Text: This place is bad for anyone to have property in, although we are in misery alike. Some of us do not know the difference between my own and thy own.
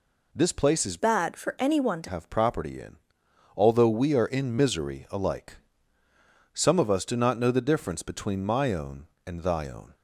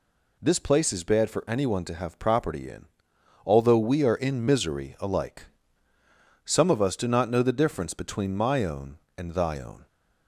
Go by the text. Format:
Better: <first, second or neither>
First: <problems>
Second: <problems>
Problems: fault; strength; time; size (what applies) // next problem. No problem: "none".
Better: second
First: changes voice from "bad" to "to"; from 0.9 to 2.0 s; 1.1 s long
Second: none